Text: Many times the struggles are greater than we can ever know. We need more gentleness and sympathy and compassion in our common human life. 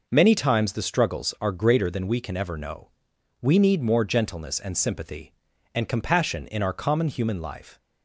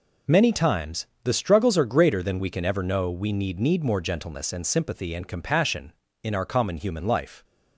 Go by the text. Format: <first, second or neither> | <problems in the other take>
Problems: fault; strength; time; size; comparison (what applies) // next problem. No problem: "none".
first | pauses between "times" and "the"; slight; at 1.0 s; 0.16 s long // says "need" twice; at 3.5 s